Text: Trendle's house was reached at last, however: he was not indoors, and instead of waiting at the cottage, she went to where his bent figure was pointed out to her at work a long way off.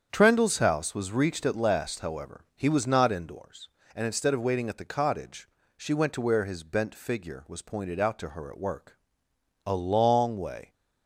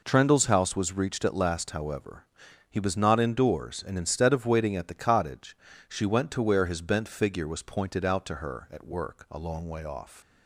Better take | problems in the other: second | starts louder than the rest; strong; until 1.1 s; 8 dB // pauses between "work" and "a"; noticeable; at 8.9 s; 0.68 s long // stops before "off"; at 10.7 s

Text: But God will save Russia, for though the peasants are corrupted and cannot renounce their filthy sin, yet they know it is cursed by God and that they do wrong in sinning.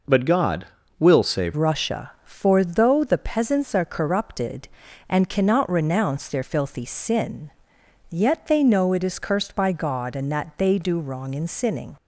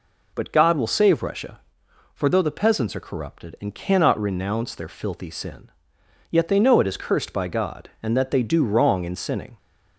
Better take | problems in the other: second | changes voice at "Russia"; from 1.5 s on; 10.4 s long

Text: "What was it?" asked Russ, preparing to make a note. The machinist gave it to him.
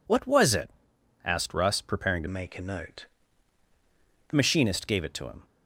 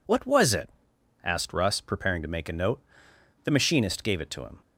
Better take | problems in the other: second | changes voice from "make" to "The"; from 2.2 to 4.3 s; 2.1 s long

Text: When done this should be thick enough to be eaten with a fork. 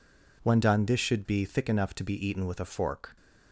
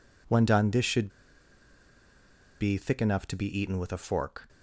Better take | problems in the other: first | pauses between "should" and "be"; strong; at 1.1 s; 1.4 s long

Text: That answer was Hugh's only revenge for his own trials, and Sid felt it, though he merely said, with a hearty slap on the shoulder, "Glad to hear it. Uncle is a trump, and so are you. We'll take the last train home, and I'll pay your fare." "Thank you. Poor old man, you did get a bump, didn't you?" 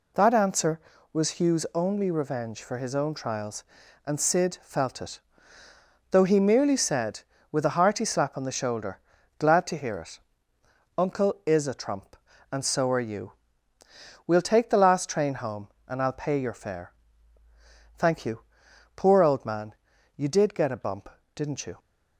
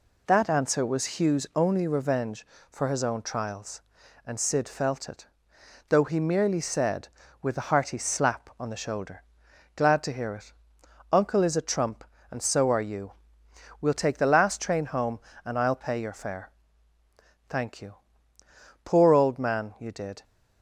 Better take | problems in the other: first | stops before "get a bump didn't you"; at 20.2 s

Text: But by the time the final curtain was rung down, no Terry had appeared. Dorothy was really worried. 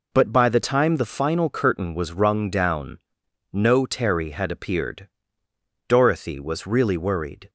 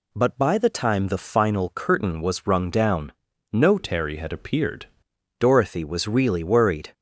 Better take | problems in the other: first | changes voice from "Terry" to "appeared"; from 3.7 to 4.8 s; 1.1 s long

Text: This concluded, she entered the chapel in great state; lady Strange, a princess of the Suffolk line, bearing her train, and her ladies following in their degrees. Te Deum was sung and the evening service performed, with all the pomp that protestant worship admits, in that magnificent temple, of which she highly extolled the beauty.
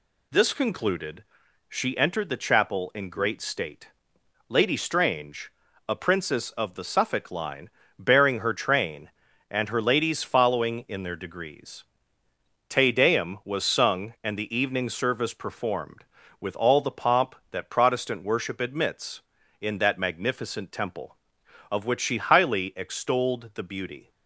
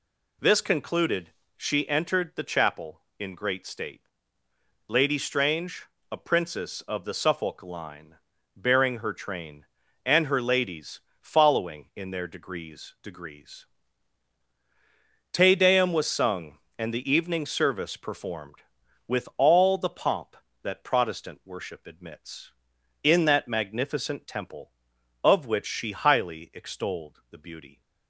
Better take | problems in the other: first | pauses between "ladies" and "following"; slight; at 11.0 s; 0.20 s long // says "degrees" twice; at 13.0 s

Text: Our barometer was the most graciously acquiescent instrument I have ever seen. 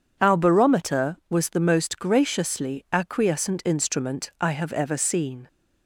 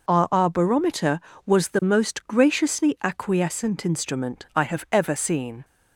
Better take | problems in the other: first | says "Our" twice; at 0.3 s

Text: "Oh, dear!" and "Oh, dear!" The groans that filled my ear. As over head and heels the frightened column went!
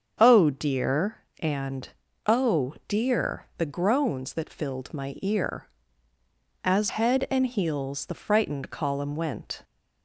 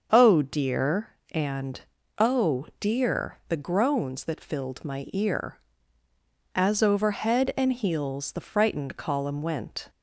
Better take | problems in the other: second | starts louder than the rest; until 1.4 s; 7 dB; also in the second // pauses between "and" and "Oh"; at 1.8 s; 0.40 s long; also in the second // skips "over"; at 6.8 s

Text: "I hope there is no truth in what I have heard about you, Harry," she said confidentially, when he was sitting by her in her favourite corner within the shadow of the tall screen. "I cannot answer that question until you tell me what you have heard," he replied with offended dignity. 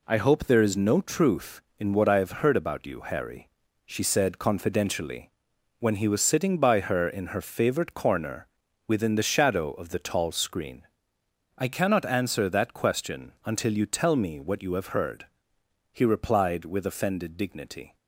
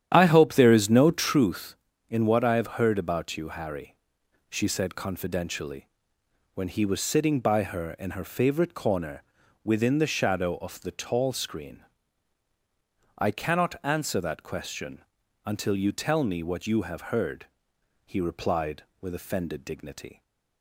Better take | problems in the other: first | starts louder than the rest; strong; until 1.4 s; 10 dB // pauses between "corner" and "within"; at 9.2 s; 0.42 s long; also in the first // pauses between "question" and "until"; at 15.0 s; 0.44 s long

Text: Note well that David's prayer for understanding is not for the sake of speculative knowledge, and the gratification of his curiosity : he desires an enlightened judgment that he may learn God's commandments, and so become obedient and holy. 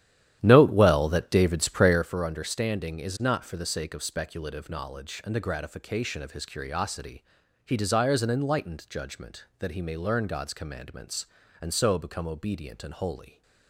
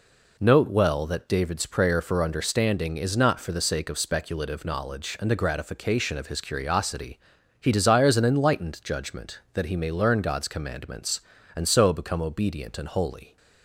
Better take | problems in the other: second | starts louder than the rest; strong; until 2.1 s; 11.5 dB

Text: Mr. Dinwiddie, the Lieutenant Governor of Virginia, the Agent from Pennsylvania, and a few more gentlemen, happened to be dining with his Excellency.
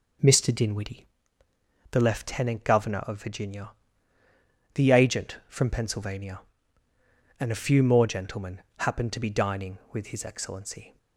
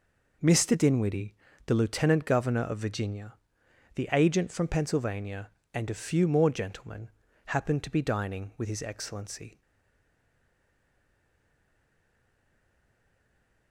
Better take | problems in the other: first | stays silent after the last word; strong; from 9.6 s on; 4.1 s long

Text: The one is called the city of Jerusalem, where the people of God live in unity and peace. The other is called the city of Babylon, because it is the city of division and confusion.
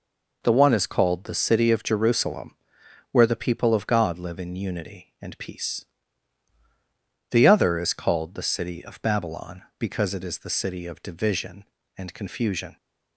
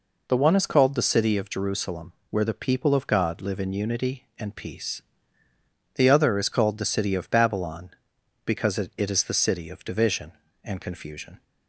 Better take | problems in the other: first | says "it" twice; at 8.9 s

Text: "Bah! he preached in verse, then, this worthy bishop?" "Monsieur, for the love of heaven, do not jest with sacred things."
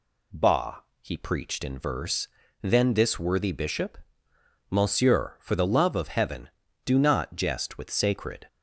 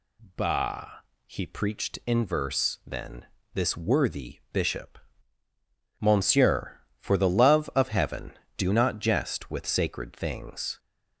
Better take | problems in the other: second | stops before "things"; at 8.4 s

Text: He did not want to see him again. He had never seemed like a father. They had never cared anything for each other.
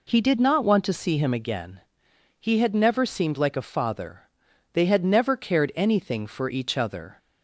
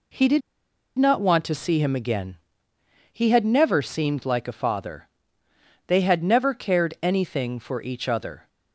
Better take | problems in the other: first | pauses between "did" and "not"; noticeable; at 0.4 s; 0.56 s long

